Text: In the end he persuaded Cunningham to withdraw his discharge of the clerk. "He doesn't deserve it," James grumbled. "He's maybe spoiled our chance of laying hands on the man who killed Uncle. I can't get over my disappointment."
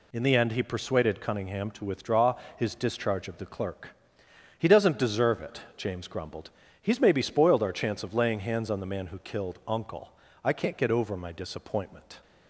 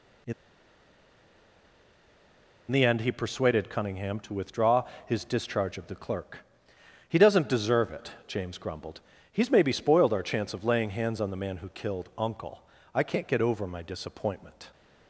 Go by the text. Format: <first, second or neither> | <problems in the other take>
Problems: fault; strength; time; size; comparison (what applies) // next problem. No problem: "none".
first | pauses between "In" and "the"; strong; at 0.3 s; 2.3 s long // pauses between "withdraw" and "his"; slight; at 4.8 s; 0.22 s long; slight in the first